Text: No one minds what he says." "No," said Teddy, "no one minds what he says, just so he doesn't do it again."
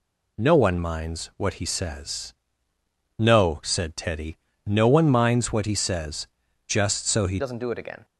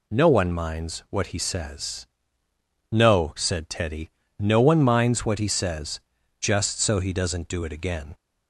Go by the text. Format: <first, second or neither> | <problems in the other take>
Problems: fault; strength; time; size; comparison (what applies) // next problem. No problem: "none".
second | changes voice at "doesn't"; from 7.3 s on; 0.7 s long